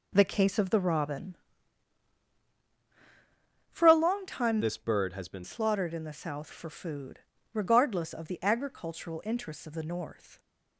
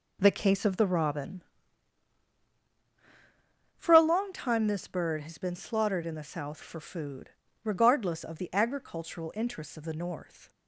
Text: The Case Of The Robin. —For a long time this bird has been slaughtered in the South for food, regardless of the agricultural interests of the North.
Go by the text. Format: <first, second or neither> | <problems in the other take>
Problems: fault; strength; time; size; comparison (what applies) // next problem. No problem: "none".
second | changes voice from "this" to "been"; from 4.6 to 5.4 s; 0.8 s long